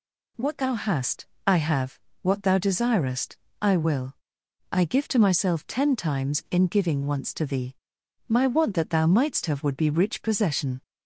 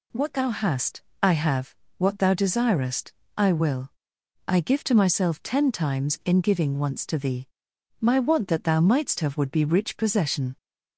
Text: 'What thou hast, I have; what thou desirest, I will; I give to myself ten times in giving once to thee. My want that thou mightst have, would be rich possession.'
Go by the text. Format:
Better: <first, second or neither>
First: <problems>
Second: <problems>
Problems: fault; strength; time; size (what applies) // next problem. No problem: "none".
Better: neither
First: none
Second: none